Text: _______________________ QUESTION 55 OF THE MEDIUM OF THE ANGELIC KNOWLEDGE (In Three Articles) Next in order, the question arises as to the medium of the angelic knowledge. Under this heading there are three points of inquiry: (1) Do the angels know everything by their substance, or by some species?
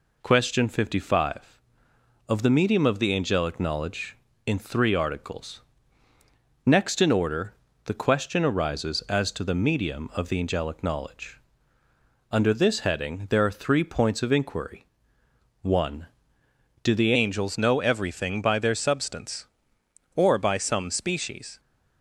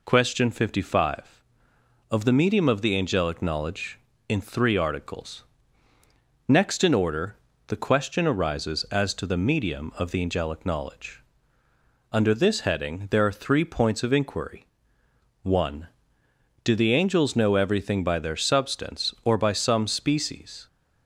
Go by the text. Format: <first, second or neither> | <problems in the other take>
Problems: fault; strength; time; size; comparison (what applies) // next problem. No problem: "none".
second | changes voice at "angels"; from 17.1 s on; 4.4 s long